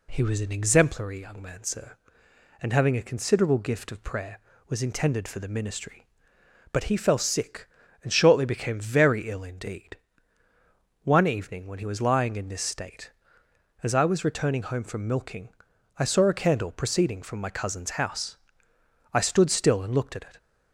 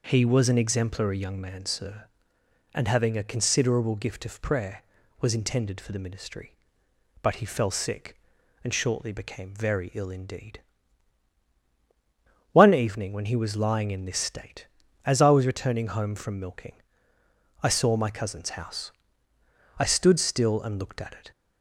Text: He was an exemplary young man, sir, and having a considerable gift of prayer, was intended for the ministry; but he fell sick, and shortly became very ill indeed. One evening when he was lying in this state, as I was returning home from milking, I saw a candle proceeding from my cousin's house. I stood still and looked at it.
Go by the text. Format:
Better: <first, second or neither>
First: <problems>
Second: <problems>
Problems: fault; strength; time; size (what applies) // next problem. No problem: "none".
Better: first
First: none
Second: skips "a candle proceeding from"; at 17.9 s